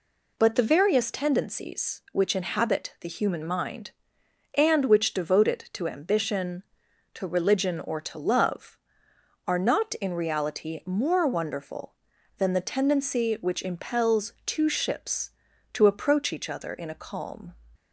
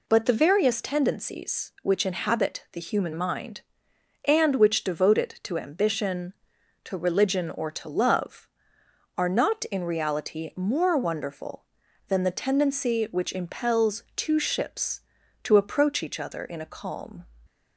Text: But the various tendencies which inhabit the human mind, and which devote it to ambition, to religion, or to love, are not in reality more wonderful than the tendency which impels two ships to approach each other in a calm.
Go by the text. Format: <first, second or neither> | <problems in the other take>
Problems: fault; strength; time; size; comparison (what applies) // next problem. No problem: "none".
neither | none